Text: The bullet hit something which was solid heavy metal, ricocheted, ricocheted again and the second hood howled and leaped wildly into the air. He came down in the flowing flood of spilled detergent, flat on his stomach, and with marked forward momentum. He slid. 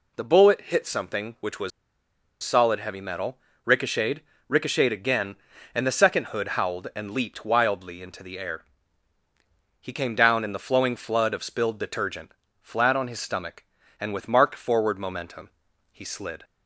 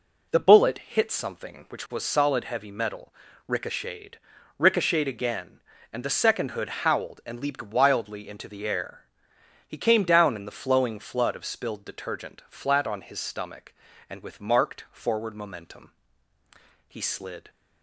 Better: second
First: pauses between "was" and "solid"; noticeable; at 1.7 s; 0.73 s long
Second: none

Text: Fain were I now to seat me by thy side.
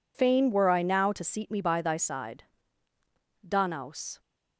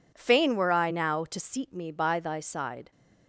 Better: second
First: goes on to say "Danaus"; noticeable; from 3.4 s on; 0.72 s long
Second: none

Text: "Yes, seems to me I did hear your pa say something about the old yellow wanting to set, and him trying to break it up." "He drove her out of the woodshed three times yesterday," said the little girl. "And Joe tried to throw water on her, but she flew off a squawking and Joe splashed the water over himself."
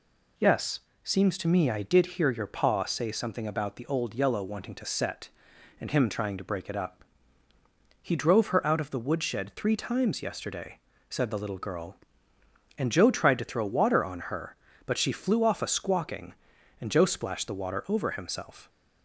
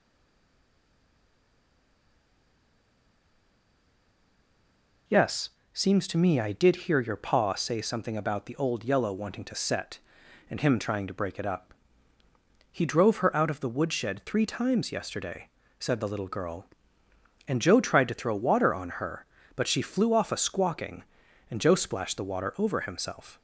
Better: first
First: none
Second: stays silent before the first word; strong; until 5.0 s; 5.0 s long

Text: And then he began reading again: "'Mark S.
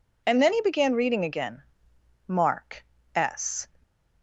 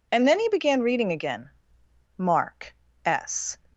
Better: neither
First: pauses between "Mark" and "S"; slight; at 2.8 s; 0.32 s long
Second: pauses between "Mark" and "S"; slight; at 2.7 s; 0.32 s long

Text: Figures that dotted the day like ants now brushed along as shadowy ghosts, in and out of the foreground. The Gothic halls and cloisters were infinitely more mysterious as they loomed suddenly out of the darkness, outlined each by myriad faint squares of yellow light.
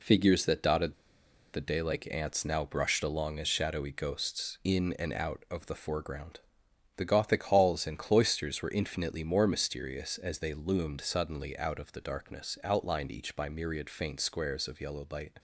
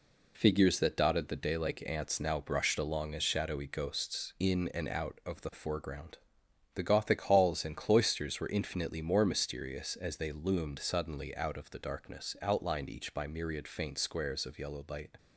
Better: second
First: pauses between "dotted" and "the"; noticeable; at 0.9 s; 0.59 s long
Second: none

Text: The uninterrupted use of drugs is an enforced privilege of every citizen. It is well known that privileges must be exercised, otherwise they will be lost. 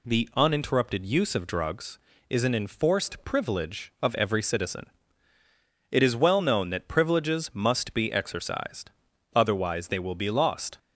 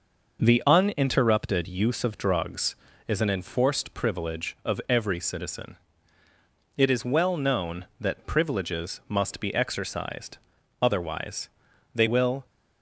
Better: first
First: none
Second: pauses between "otherwise" and "they"; at 11.4 s; 0.44 s long // stops before "be lost"; at 12.4 s

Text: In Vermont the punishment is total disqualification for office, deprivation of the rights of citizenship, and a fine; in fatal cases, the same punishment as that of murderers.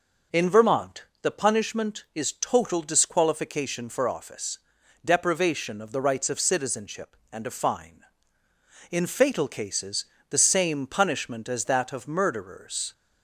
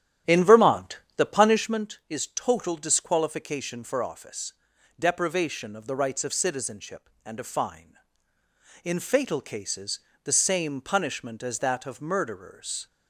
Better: first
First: pauses between "Vermont" and "the"; slight; at 1.0 s; 0.18 s long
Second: starts louder than the rest; strong; until 1.9 s; 11 dB // pauses between "Vermont" and "the"; slight; at 0.9 s; 0.18 s long

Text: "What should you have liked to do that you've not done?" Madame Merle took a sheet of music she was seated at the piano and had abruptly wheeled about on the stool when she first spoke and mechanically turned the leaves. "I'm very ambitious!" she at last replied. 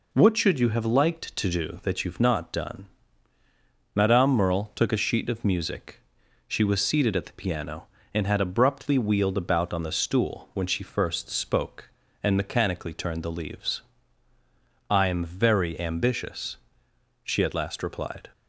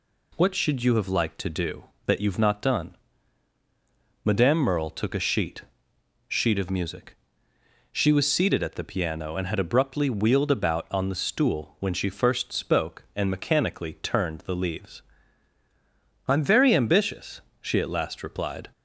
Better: first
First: pauses between "music" and "she"; noticeable; at 6.0 s; 0.48 s long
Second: says "sheet" twice; at 6.2 s // pauses between "music" and "she"; noticeable; at 7.1 s; 0.76 s long

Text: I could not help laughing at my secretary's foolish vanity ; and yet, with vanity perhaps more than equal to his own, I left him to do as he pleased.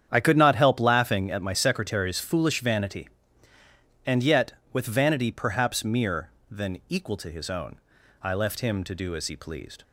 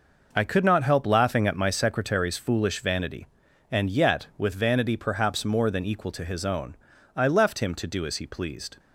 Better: second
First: starts louder than the rest; strong; until 1.1 s; 9 dB // says "mere" for "more"; at 5.8 s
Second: none

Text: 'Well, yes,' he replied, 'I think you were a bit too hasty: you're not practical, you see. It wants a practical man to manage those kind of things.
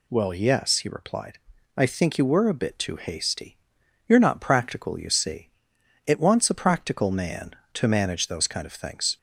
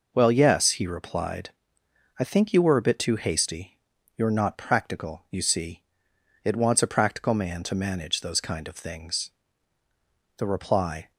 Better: first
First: none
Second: goes on to say "The reply"; noticeable; from 10.3 s on; 0.74 s long

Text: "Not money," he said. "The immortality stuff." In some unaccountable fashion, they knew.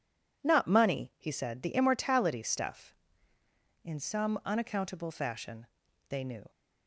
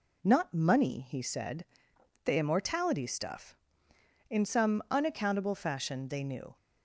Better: neither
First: none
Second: none

